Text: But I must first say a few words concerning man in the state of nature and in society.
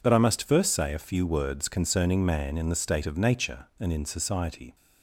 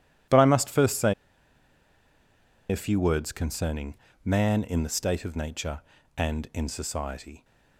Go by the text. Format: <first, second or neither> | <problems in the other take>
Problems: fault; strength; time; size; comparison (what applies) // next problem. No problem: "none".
first | pauses between "say" and "a"; strong; at 1.1 s; 1.5 s long // pauses between "concerning" and "man"; slight; at 3.9 s; 0.30 s long